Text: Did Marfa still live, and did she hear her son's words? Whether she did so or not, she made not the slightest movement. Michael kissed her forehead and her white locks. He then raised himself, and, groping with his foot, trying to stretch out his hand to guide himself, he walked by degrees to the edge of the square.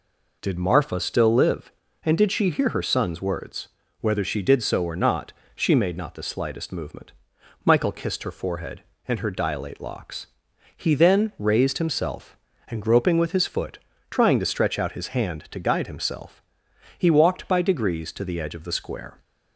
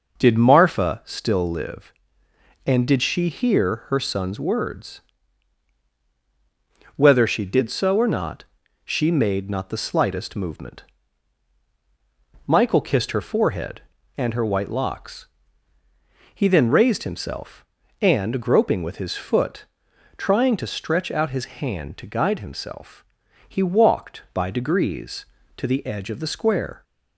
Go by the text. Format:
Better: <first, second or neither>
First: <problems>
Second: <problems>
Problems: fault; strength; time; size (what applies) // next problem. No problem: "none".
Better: second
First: says "dilate" for "white"; at 9.2 s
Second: none